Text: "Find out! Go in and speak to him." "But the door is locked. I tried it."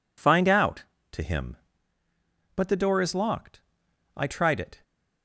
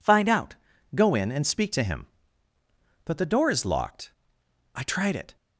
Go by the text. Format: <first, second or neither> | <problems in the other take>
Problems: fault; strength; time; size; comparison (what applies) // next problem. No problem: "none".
second | skips "Go in and speak"; at 0.9 s